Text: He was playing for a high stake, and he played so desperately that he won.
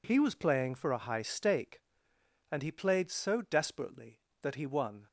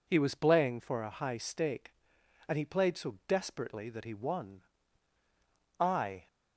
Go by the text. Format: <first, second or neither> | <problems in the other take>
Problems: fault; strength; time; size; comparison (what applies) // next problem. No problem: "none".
first | goes on to say "I"; slight; from 5.7 s on; 0.48 s long